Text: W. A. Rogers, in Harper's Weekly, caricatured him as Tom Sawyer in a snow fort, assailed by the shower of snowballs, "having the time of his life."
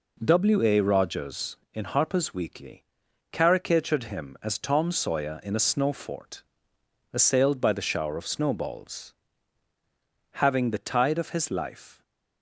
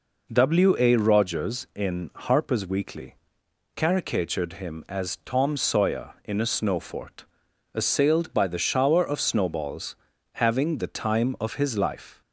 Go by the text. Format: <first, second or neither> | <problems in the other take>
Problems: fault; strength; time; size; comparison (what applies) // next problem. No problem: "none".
second | says "tide" for "time"; at 10.8 s